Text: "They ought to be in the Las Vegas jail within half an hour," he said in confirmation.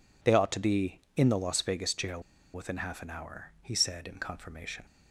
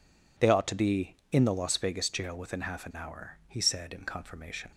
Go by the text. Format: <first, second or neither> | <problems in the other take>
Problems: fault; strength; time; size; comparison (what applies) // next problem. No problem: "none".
second | pauses between "jail" and "within"; slight; at 2.2 s; 0.32 s long